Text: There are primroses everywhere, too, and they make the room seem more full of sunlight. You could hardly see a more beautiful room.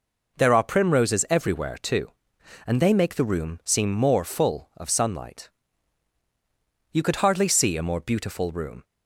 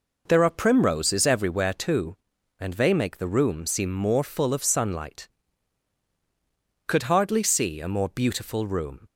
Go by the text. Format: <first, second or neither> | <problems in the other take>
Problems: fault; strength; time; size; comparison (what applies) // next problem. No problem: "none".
first | skips "You"; at 6.0 s